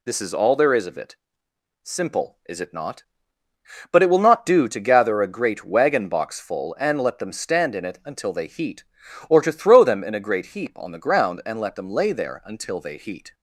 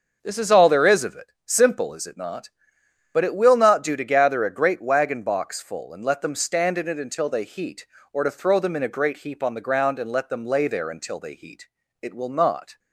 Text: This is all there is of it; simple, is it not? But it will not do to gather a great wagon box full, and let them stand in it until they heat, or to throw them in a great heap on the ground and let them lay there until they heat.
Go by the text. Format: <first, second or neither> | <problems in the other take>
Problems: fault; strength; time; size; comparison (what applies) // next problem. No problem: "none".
first | starts louder than the rest; until 1.2 s; 6 dB // goes on to say "It will not"; noticeable; from 12.0 s on; 0.76 s long